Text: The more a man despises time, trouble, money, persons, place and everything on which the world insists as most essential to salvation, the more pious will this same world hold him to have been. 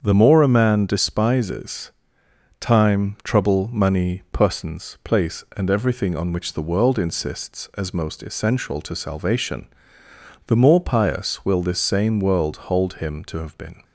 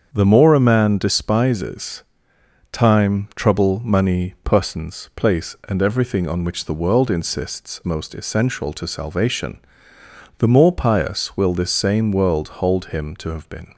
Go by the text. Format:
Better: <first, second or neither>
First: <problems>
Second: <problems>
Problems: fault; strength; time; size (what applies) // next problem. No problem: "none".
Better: first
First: starts louder than the rest; strong; until 1.0 s; 7 dB // pauses between "despises" and "time"; noticeable; at 1.9 s; 0.70 s long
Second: starts louder than the rest; until 1.1 s; 7 dB // pauses between "despises" and "time"; noticeable; at 2.0 s; 0.70 s long // skips "as"; at 7.8 s